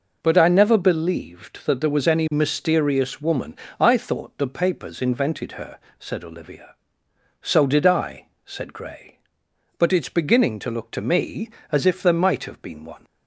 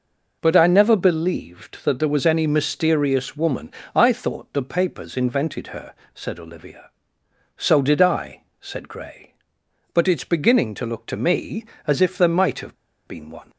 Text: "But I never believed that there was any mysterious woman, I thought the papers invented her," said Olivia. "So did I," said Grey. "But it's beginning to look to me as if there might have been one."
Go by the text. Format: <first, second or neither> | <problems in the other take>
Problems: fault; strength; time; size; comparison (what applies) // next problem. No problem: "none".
first | pauses between "have" and "been"; slight; at 12.7 s; 0.32 s long